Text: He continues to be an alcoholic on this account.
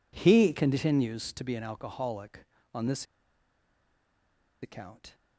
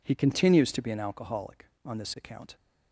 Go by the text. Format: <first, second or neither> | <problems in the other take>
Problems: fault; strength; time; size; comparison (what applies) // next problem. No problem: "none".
second | pauses between "this" and "account"; strong; at 3.0 s; 1.5 s long